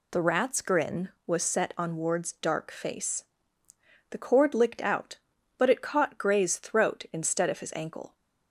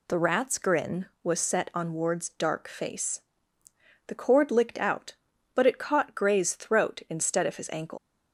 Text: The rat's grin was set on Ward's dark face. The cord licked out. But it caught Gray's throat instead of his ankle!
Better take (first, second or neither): first